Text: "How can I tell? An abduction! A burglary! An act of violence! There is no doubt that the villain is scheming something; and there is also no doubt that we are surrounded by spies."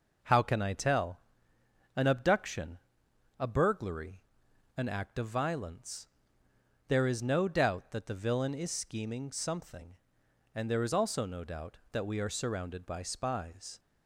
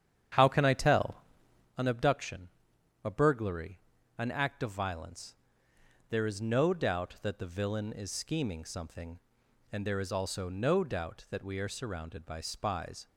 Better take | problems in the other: first | starts louder than the rest; strong; until 1.7 s; 9.5 dB

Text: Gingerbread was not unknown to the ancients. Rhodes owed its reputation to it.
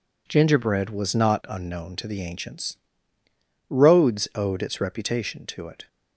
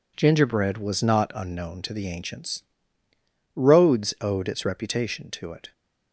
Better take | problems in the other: neither | none

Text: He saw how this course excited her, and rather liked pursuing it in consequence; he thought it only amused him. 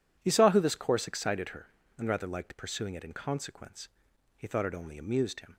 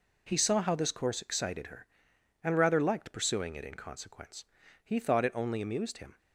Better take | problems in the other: second | says "who" for "how"; at 0.4 s

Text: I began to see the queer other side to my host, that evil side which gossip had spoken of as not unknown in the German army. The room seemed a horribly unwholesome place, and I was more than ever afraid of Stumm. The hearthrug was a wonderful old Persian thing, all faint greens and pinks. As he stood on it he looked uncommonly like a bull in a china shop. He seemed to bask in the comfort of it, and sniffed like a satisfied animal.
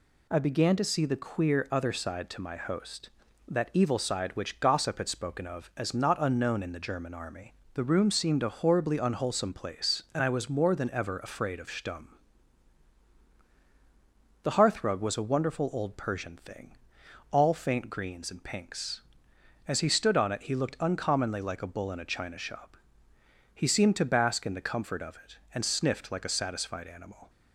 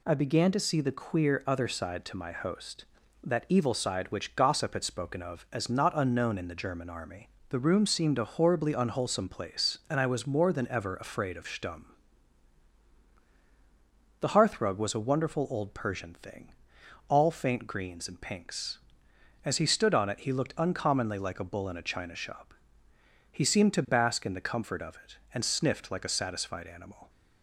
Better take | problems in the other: neither | none

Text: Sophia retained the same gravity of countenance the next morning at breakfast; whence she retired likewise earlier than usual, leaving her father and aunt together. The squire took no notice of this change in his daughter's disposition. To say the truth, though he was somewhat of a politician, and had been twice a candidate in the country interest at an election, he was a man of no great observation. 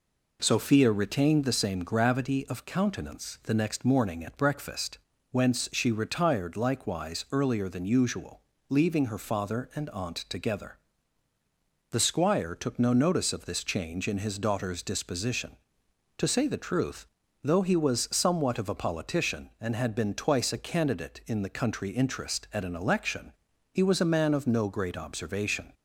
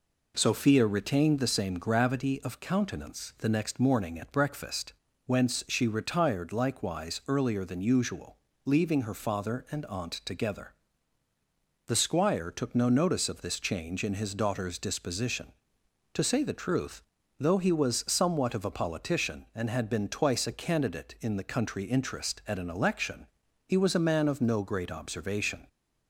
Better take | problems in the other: neither | none

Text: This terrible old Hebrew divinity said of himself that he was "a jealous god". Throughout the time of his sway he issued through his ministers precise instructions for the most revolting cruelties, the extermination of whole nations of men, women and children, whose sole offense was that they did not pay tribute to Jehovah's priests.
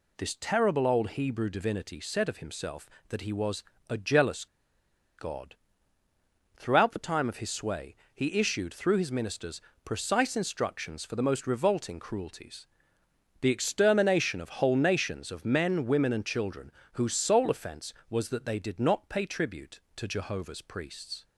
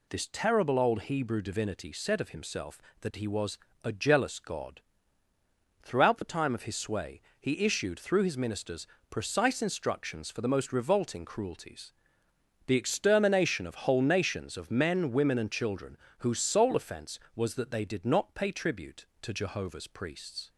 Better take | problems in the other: second | pauses between "was" and "a"; slight; at 3.6 s; 0.26 s long; slight in the second // pauses between "jealous" and "god"; noticeable; at 4.4 s; 0.72 s long // pauses between "sway" and "he"; slight; at 7.9 s; 0.20 s long; slight in the second // pauses between "ministers" and "precise"; slight; at 9.6 s; 0.20 s long; slight in the second

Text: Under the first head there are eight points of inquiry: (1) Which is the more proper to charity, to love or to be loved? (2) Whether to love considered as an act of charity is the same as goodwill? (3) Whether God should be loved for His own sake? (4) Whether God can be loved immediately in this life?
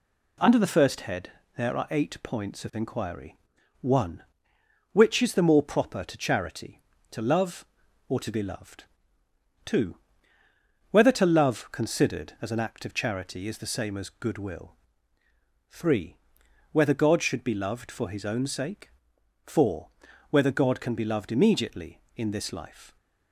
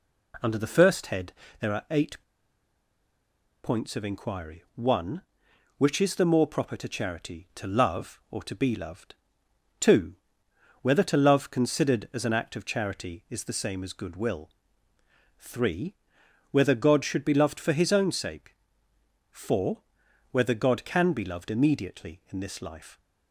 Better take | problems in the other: first | pauses between "head" and "there"; slight; at 1.3 s; 0.26 s long; slight in the first // pauses between "eight" and "points"; strong; at 2.2 s; 1.4 s long

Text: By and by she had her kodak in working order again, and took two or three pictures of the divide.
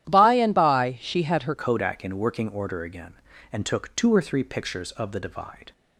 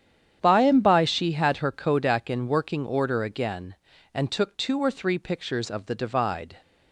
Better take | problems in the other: second | starts louder than the rest; strong; until 1.1 s; 11.5 dB; strong in the second // changes voice at "kodak"; from 1.5 s on; 4.2 s long

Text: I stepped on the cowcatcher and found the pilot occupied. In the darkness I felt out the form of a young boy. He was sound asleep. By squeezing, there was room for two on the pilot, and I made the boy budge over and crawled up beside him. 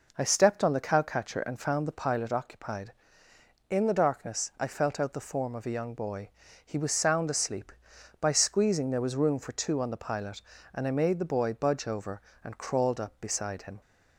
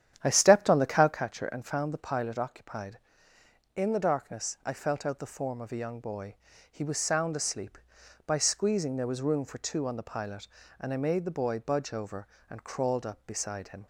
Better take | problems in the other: first | starts louder than the rest; strong; until 1.2 s; 10 dB

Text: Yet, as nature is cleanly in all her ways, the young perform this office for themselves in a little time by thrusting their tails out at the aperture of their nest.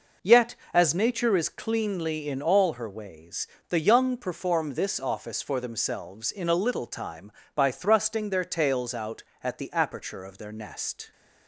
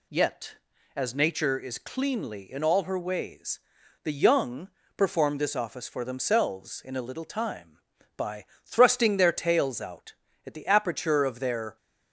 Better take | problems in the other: first | pauses between "young" and "perform"; slight; at 4.6 s; 0.28 s long // pauses between "by" and "thrusting"; slight; at 8.4 s; 0.20 s long // stops before "nest"; at 11.7 s

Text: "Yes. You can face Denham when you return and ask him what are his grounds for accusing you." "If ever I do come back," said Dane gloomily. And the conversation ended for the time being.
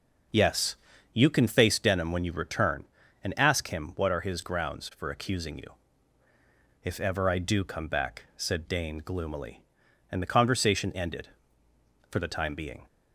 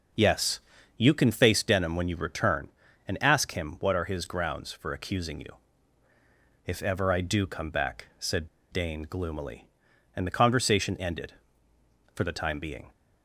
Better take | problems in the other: first | pauses between "said" and "Dane"; slight; at 8.4 s; 0.23 s long

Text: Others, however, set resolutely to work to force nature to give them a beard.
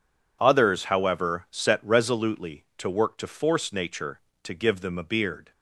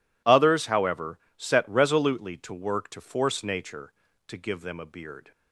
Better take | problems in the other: neither | none

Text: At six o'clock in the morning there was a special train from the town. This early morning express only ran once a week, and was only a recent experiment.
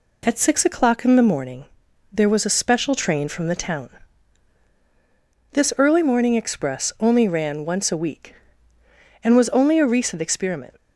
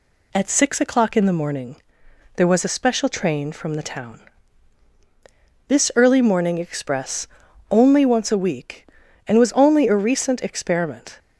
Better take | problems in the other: first | pauses between "morning" and "there"; noticeable; at 1.7 s; 0.62 s long; also in the first // pauses between "express" and "only"; at 7.2 s; 0.42 s long // skips "ran"; at 8.0 s

